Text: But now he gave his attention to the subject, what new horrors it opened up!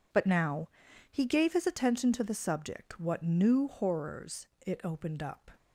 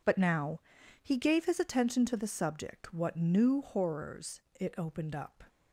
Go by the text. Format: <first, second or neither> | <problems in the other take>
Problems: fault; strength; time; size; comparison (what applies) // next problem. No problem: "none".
neither | pauses between "now" and "he"; the same in both // pauses between "horrors" and "it"; slight; the same in both